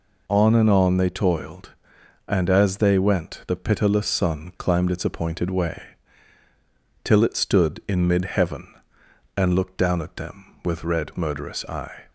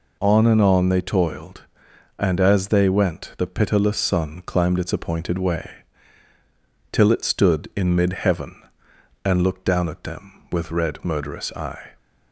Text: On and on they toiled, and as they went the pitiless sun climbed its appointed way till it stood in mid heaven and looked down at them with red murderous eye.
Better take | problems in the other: neither | pauses between "way" and "till"; the same in both

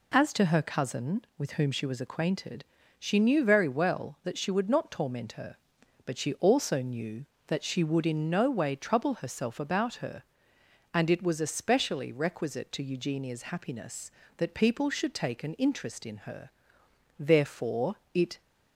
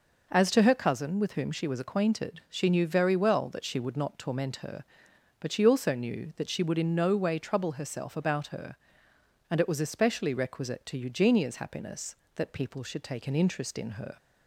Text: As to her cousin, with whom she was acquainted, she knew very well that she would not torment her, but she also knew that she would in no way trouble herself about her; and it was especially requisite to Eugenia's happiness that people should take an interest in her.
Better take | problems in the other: second | goes on to say "Therefore it"; noticeable; from 17.1 s on; 1.2 s long

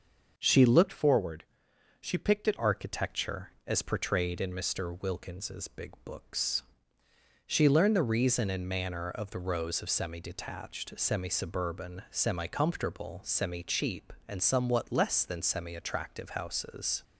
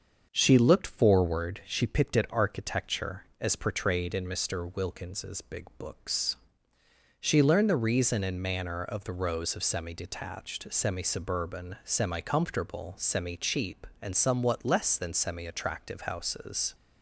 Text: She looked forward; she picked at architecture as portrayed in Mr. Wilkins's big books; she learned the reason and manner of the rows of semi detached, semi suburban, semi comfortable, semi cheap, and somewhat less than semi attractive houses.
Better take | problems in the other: second | starts louder than the rest; noticeable; until 1.3 s; 6 dB; also in the second // changes voice from "forward" to "at"; from 0.9 to 2.5 s; 1.6 s long

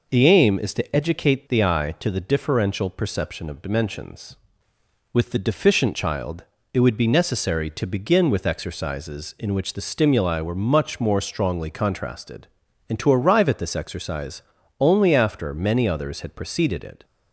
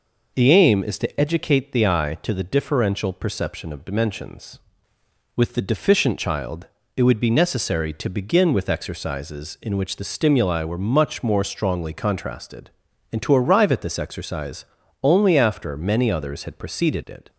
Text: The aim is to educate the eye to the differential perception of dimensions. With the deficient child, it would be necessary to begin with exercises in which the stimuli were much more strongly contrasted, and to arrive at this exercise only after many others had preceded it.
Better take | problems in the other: neither | pauses between "exercise" and "only"; the same in both

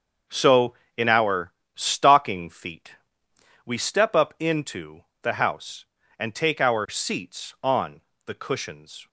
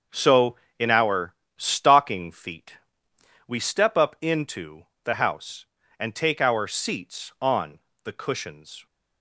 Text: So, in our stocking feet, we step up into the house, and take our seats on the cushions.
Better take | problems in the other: neither | starts louder than the rest; the same in both // pauses between "our" and "stocking"; slight; the same in both // pauses between "into" and "the"; slight; the same in both // pauses between "on" and "the"; slight; the same in both

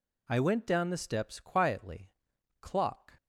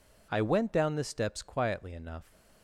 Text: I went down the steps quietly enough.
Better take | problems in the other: second | says "clock" for "enough"; at 2.6 s

